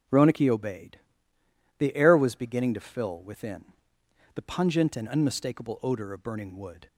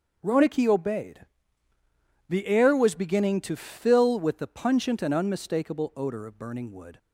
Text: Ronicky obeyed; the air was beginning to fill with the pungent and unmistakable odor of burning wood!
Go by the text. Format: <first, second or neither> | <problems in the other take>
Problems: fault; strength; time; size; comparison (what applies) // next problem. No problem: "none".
second | starts louder than the rest; until 1.8 s; 7 dB; noticeable in the second // says "within" for "with"; at 3.2 s